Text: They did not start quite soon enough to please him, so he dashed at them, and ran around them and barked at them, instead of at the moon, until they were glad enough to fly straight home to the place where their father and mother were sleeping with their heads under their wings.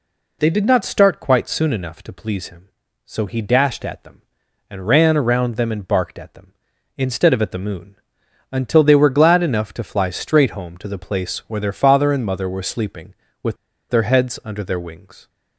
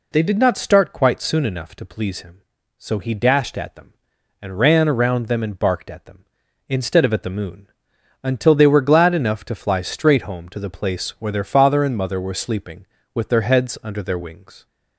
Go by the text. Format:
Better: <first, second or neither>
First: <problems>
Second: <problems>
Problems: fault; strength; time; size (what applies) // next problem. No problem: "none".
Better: second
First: pauses between "with" and "their"; slight; at 13.5 s; 0.34 s long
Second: none